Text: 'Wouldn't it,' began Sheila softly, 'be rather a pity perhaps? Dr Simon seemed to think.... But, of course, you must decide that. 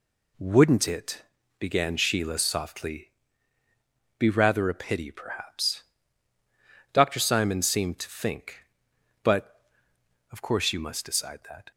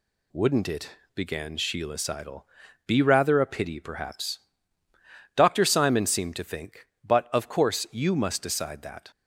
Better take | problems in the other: first | says "seidel" for "softly"; at 1.9 s

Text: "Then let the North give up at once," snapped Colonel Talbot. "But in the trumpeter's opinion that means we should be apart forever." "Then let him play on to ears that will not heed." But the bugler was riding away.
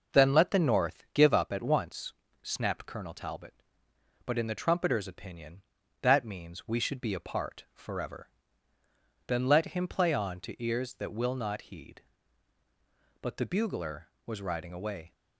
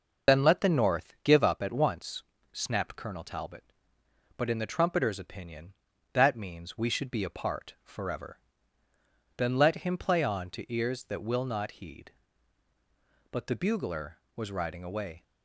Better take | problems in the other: first | loses the start of "Then"; at 0.2 s; 55 ms

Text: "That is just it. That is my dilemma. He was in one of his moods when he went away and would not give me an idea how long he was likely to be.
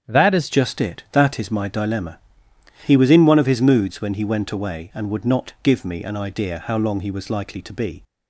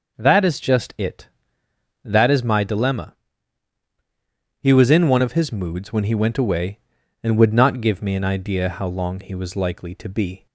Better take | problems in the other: second | starts louder than the rest; strong; until 1.1 s; 8.5 dB // changes voice at "just"; from 0.5 s on; 7.5 s long

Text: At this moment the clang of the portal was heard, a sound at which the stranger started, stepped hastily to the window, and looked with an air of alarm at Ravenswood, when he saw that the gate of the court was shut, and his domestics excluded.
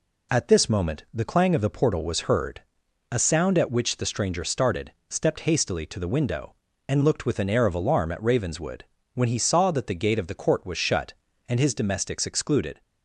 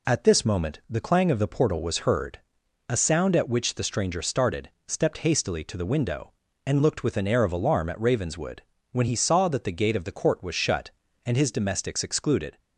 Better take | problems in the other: neither | none

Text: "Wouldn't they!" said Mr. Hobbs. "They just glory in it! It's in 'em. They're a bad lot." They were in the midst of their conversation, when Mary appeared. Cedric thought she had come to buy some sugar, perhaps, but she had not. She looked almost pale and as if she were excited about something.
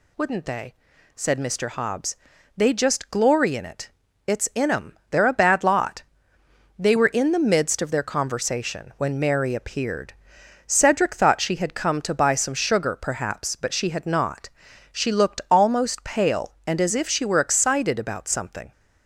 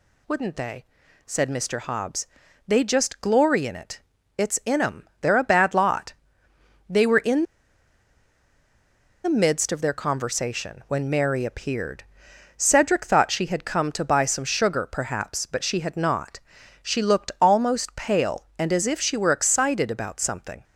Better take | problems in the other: first | pauses between "in" and "the"; strong; at 7.4 s; 1.8 s long

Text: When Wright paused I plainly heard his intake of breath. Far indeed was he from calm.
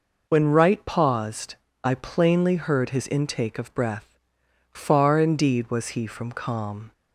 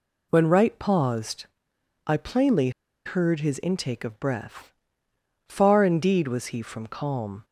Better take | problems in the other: first | pauses between "paused" and "I"; noticeable; at 1.4 s; 0.60 s long; slight in the first // pauses between "plainly" and "heard"; slight; at 2.6 s; 0.35 s long

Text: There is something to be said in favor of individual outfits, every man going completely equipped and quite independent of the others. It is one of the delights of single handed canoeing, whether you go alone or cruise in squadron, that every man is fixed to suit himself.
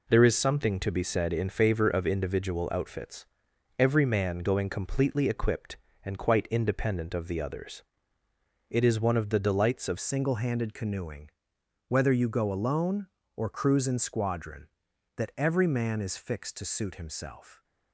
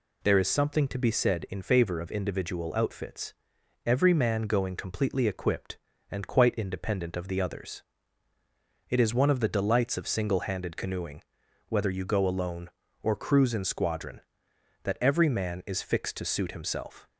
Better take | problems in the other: second | changes voice at "single"; from 9.9 s on; 7.7 s long

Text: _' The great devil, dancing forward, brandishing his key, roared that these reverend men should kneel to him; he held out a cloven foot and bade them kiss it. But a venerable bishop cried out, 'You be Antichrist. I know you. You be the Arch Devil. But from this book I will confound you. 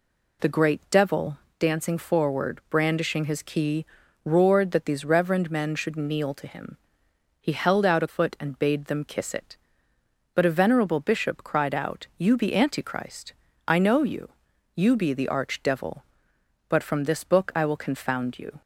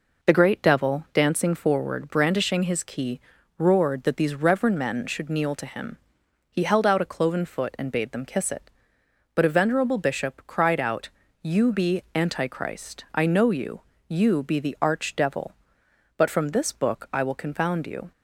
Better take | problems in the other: second | skips "cloven"; at 8.0 s

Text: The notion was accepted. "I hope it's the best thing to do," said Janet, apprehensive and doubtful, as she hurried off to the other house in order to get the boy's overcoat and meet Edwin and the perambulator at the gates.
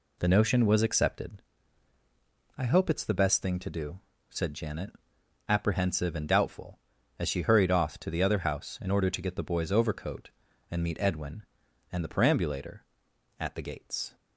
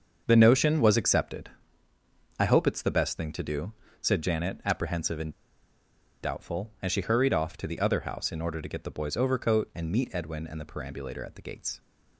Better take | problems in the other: first | starts louder than the rest; until 1.2 s; 6.5 dB // pauses between "and" and "doubtful"; noticeable; at 5.3 s; 0.92 s long

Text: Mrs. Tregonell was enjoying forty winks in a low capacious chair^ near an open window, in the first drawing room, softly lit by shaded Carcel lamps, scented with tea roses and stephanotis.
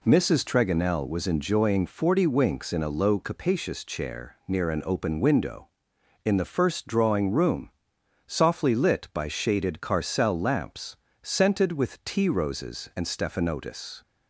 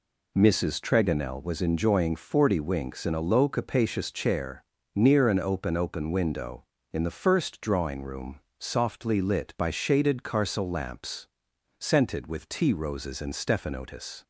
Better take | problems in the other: first | pauses between "chair" and "near"; slight; at 4.6 s; 0.32 s long // says "open" twice; at 5.7 s

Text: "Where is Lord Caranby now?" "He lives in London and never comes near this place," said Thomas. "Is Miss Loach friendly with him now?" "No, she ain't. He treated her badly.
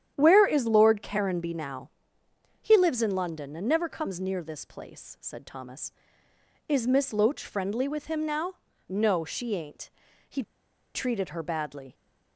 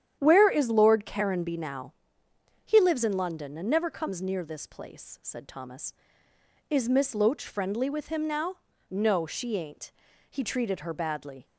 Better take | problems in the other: second | starts louder than the rest; strong; until 1.1 s; 9.5 dB; strong in the second // pauses between "He" and "treated"; noticeable; at 10.4 s; 0.53 s long

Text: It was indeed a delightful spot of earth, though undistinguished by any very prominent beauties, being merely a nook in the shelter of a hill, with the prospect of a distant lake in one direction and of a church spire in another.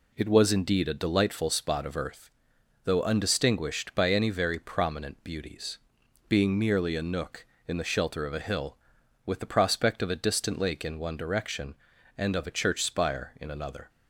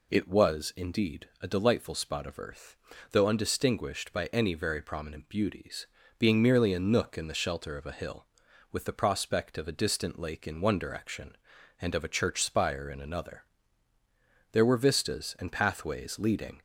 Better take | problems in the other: first | goes on to say "There were vistas and pathways leading"; strong; from 14.5 s on; 2.0 s long

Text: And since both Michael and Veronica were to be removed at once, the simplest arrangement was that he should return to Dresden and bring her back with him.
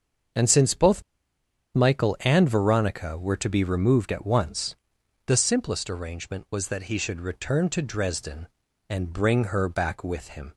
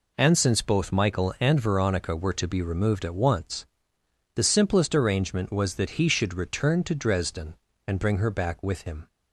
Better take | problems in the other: second | starts louder than the rest; until 2.0 s; 6.5 dB // pauses between "both" and "Michael"; noticeable; at 1.0 s; 0.73 s long

